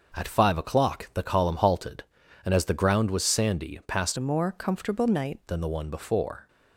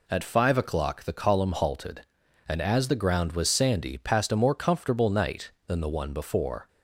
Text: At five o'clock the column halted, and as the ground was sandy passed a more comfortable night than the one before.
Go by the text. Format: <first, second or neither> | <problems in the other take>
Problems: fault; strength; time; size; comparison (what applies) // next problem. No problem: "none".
second | changes voice from "a" to "night"; from 4.1 to 5.3 s; 1.2 s long